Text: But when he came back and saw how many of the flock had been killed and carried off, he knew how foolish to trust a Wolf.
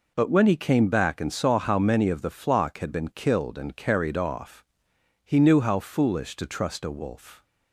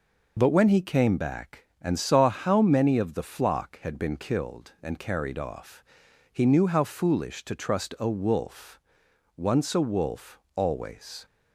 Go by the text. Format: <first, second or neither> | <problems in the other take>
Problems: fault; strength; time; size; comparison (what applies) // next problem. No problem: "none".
first | goes on to say "Once a wolf always"; strong; from 9.3 s on; 1.9 s long